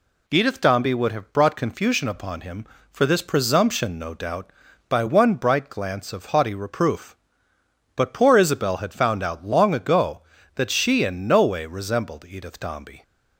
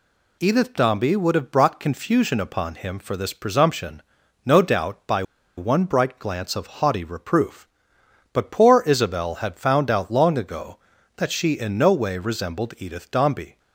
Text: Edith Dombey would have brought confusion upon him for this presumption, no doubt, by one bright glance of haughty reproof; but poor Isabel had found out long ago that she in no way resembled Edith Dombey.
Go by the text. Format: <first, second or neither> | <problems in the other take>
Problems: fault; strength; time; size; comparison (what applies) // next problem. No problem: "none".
first | pauses between "by" and "one"; slight; at 5.2 s; 0.35 s long